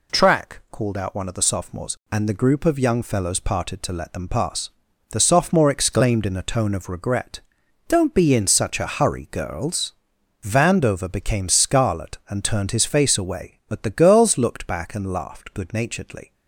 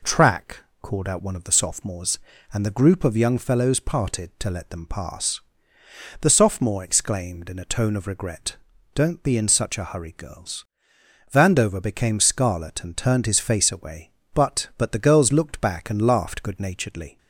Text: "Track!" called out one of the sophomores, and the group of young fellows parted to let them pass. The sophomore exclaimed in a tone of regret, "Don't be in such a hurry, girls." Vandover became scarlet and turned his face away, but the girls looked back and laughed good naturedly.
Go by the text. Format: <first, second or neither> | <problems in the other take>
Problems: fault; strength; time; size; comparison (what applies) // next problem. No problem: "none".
first | says "but" twice; at 14.7 s